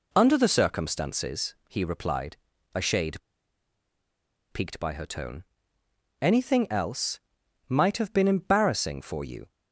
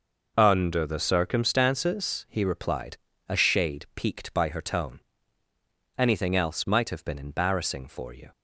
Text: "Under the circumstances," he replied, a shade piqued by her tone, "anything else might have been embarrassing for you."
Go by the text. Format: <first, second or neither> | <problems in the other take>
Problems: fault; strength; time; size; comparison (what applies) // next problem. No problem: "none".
second | pauses between "shade" and "piqued"; strong; at 3.1 s; 1.3 s long // pauses between "else" and "might"; noticeable; at 7.1 s; 0.48 s long